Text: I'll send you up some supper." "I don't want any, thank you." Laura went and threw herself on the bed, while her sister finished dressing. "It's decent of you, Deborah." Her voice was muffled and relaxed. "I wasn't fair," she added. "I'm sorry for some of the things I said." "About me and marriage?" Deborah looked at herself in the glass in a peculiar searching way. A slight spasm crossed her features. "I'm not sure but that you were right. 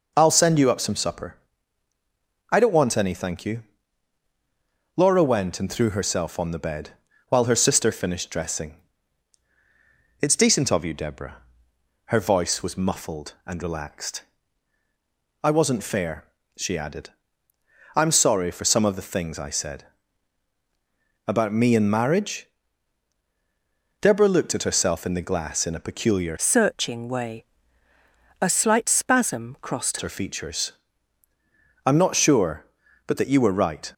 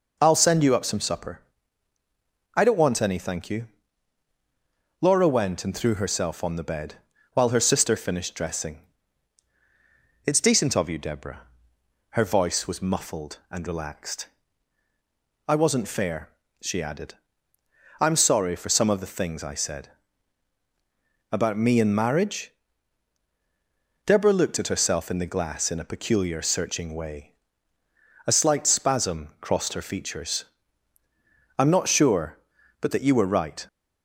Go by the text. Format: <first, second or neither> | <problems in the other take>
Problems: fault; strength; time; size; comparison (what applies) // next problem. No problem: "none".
second | changes voice from "searching" to "crossed"; from 26.3 to 29.9 s; 3.6 s long